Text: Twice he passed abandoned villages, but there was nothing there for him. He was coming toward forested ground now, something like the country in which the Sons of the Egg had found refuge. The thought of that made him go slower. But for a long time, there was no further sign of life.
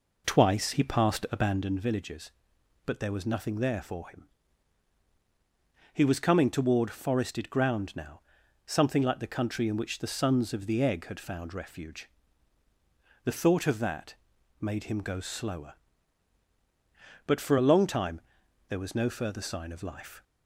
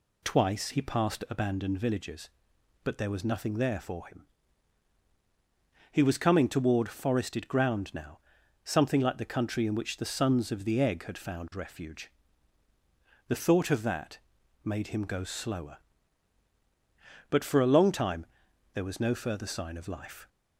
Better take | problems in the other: second | starts louder than the rest; noticeable; until 1.7 s; 4.5 dB // pauses between "that" and "made"; noticeable; at 14.1 s; 0.46 s long; noticeable in the second

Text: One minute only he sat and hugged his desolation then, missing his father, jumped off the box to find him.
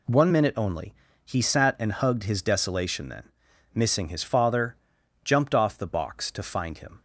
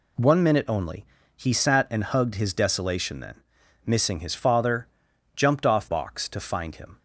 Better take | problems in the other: first | pauses between "only" and "he"; slight; at 1.0 s; 0.32 s long; slight in the first // skips "the"; at 5.8 s

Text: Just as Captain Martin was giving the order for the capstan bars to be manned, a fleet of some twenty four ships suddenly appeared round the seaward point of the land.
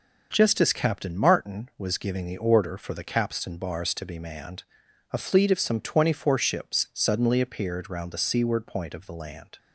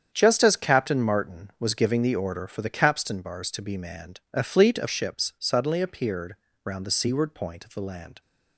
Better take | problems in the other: first | starts louder than the rest; strong; until 1.1 s; 8 dB // skips "some twenty four"; at 4.8 s // pauses between "appeared" and "round"; slight; at 6.3 s; 0.30 s long

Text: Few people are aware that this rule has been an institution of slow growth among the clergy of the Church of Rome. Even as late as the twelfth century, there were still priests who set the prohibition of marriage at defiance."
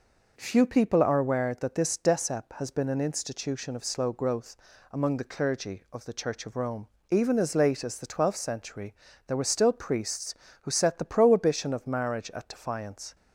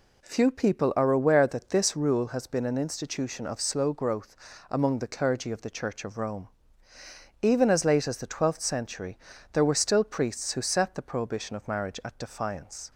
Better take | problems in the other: second | says "decep" for "rule"; at 1.9 s // pauses between "growth" and "among"; at 4.5 s; 0.38 s long; slight in the second

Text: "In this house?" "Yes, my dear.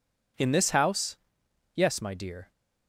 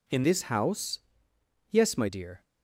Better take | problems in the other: first | changes voice from "this" to "my"; from 0.2 to 2.0 s; 1.8 s long

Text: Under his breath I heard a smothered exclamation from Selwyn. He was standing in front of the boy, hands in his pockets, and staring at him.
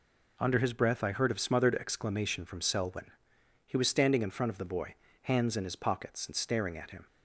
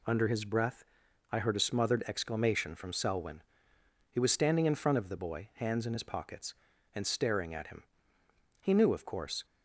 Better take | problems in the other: first | pauses between "breath" and "I"; noticeable; at 0.8 s; 0.48 s long // goes on to say "He knew of course"; noticeable; from 8.6 s on; 0.84 s long

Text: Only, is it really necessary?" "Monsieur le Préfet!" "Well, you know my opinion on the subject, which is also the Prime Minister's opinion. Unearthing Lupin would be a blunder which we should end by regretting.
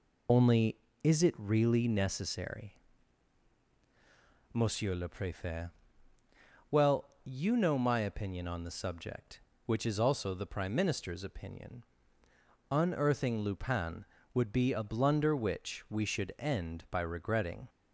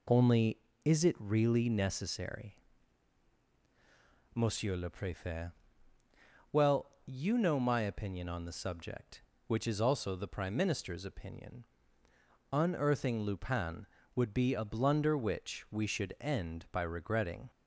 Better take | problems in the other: second | loses the start of "Only"; at 0.2 s; 40 ms

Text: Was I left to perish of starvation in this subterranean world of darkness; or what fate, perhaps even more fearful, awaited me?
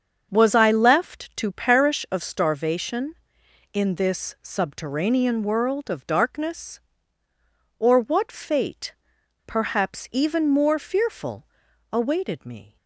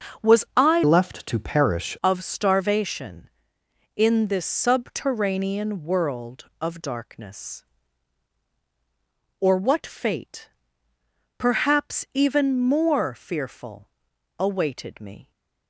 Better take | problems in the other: first | starts louder than the rest; until 1.3 s; 6.5 dB; also in the first // changes voice from "left" to "perish"; from 0.8 to 1.9 s; 1.1 s long

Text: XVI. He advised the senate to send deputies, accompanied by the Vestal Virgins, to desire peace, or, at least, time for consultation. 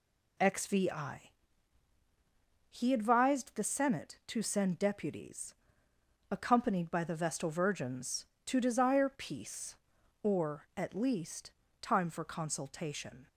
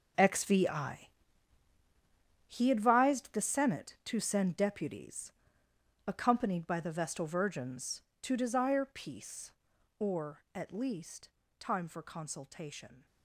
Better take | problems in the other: first | gets quieter; strong; throughout; 13 dB

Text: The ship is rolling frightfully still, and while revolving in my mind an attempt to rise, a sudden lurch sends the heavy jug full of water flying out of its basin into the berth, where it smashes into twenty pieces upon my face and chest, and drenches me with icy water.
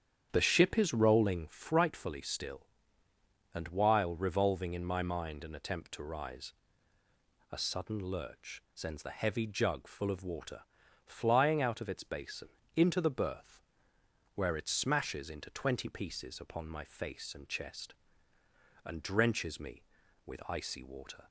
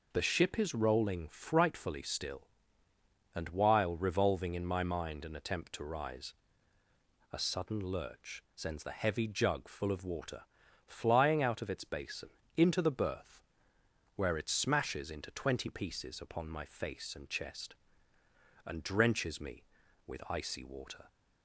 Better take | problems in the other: second | starts louder than the rest; strong; until 1.5 s; 9 dB // pauses between "water" and "flying"; at 10.5 s; 0.44 s long; also in the second // pauses between "basin" and "into"; slight; at 12.4 s; 0.26 s long; slight in the second

